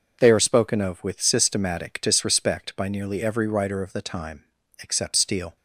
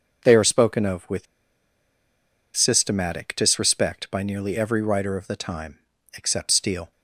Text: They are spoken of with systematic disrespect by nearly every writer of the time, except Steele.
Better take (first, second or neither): first